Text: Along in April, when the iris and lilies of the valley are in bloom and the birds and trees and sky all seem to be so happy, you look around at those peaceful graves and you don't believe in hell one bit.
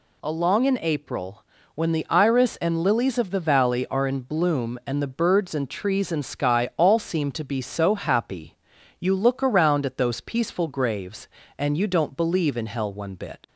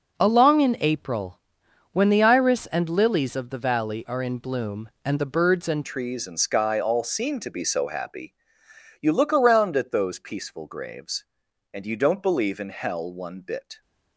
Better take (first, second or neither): first